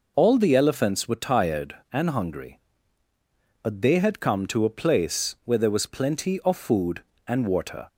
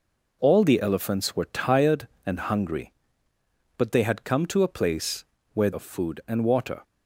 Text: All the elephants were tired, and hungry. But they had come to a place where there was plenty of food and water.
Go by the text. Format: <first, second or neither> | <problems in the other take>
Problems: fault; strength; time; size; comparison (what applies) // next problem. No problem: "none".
first | pauses between "place" and "where"; slight; at 5.2 s; 0.30 s long // skips "there was plenty"; at 5.7 s